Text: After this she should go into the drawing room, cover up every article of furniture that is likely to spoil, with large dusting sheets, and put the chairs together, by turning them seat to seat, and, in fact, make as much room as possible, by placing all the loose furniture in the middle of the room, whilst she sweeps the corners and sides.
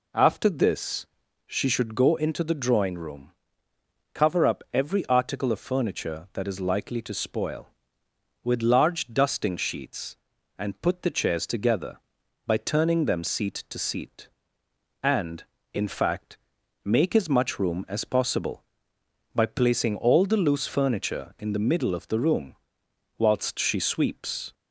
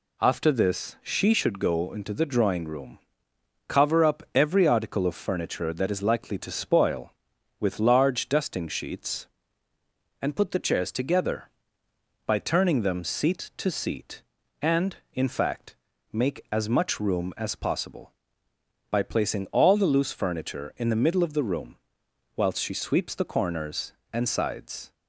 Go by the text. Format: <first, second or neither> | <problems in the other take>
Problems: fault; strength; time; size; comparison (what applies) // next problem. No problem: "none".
second | pauses between "this" and "she"; at 1.0 s; 0.40 s long // stops before "the corners and sides"; at 24.5 s